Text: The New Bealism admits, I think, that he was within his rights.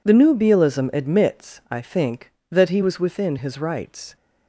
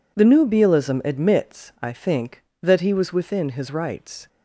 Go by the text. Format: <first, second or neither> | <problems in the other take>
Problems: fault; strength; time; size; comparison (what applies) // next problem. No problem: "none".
neither | none